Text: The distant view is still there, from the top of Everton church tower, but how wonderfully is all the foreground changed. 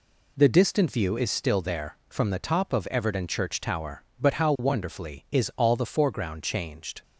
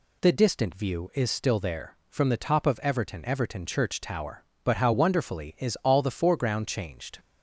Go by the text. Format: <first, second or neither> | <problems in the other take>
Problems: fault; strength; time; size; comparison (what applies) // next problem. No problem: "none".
first | says "Everton" twice; at 3.2 s